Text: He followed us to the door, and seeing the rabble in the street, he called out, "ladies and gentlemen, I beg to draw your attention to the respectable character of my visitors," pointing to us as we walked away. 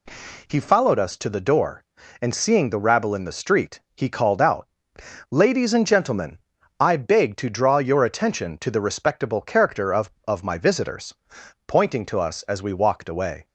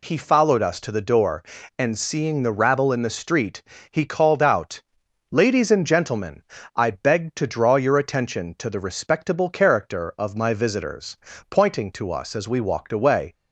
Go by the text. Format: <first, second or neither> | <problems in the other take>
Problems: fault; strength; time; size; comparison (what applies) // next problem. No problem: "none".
second | says "of" twice; at 10.2 s